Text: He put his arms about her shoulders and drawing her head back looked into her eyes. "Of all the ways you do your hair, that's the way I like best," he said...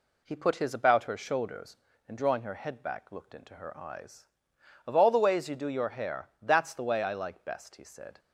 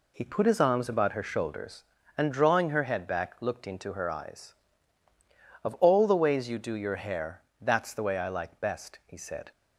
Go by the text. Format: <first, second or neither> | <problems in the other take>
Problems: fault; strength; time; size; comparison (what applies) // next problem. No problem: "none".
second | skips "arms"; at 0.7 s